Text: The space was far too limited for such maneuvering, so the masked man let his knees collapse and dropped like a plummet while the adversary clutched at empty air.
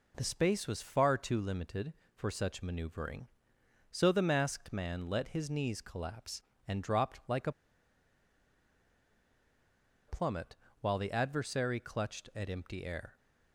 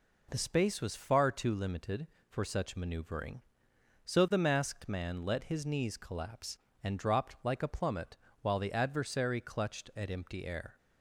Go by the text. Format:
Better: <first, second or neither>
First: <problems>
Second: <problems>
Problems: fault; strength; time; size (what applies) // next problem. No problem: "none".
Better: second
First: pauses between "a" and "plummet"; strong; at 7.5 s; 2.5 s long // pauses between "plummet" and "while"; slight; at 10.5 s; 0.26 s long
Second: pauses between "plummet" and "while"; slight; at 8.1 s; 0.26 s long